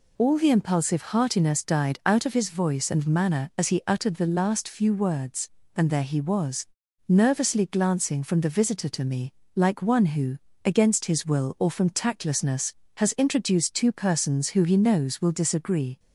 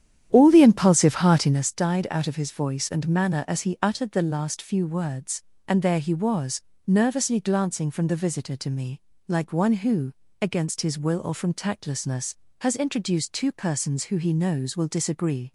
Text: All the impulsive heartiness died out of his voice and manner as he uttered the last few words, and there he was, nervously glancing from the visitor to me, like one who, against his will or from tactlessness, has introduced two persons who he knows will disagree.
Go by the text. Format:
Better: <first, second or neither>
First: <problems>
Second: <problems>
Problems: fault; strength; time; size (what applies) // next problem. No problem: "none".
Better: first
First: none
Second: starts louder than the rest; strong; until 1.7 s; 10 dB